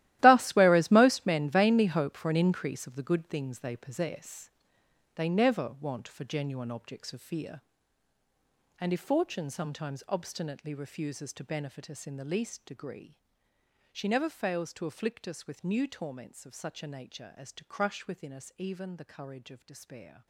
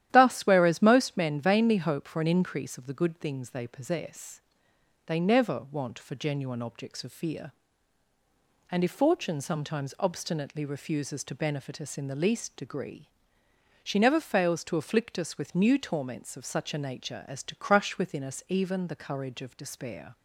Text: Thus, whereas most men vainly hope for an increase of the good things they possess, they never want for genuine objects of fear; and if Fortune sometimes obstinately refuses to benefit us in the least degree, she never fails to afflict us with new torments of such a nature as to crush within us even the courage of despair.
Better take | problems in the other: second | gets quieter; strong; throughout; 14.5 dB // starts louder than the rest; strong; until 1.2 s; 15 dB; strong in the second

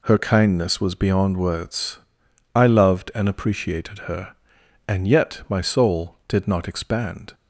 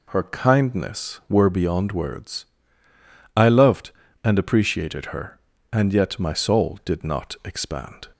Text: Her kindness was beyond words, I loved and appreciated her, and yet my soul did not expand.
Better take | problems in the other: first | says "were" for "was"; at 1.2 s

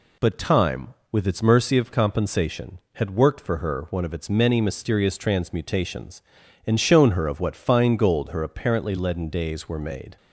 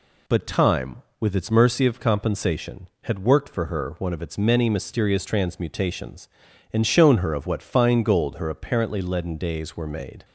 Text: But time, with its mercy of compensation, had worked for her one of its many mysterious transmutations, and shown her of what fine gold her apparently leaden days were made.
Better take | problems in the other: neither | none

